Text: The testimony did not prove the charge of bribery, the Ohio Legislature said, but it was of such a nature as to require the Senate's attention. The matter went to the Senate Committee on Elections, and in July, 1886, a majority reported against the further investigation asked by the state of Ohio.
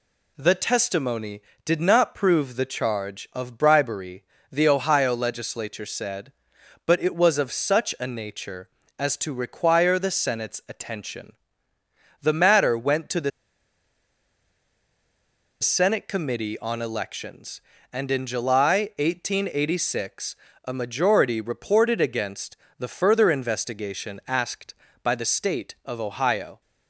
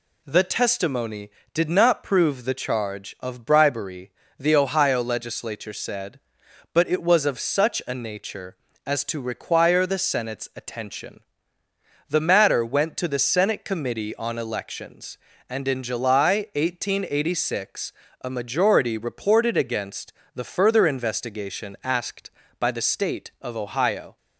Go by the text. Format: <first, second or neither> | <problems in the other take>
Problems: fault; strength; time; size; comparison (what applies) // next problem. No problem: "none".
second | pauses between "the" and "Senate"; strong; at 13.2 s; 2.3 s long // pauses between "against" and "the"; slight; at 22.5 s; 0.22 s long; slight in the second